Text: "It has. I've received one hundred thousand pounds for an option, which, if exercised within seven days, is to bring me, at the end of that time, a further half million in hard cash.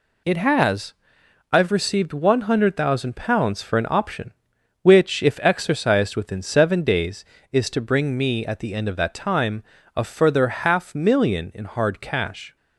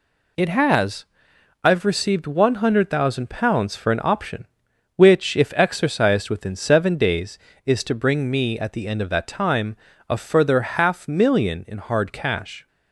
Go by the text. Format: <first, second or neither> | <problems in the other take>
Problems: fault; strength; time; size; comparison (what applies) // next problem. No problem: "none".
neither | none